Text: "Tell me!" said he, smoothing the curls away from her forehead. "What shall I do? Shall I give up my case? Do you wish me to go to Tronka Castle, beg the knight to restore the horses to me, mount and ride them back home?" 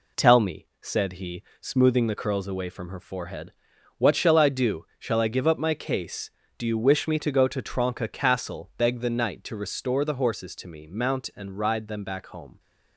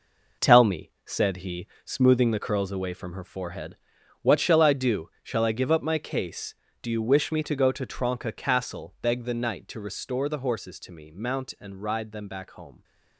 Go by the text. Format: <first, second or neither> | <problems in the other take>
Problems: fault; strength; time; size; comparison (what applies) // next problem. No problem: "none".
first | gets quieter; strong; throughout; 8 dB